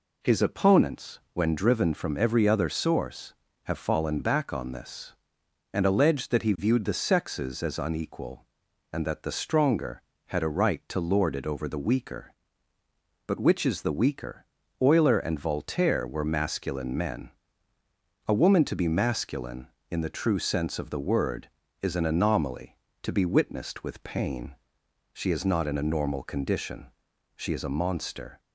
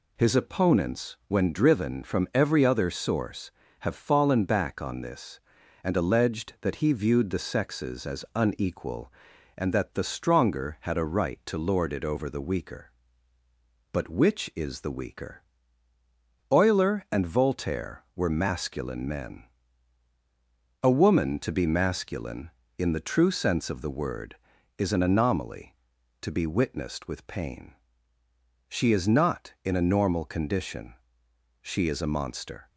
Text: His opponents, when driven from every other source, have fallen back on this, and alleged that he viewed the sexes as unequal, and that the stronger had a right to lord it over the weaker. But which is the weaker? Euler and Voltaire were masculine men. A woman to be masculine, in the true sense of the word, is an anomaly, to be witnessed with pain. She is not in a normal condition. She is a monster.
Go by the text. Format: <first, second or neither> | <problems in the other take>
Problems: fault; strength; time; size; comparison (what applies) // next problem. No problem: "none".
neither | none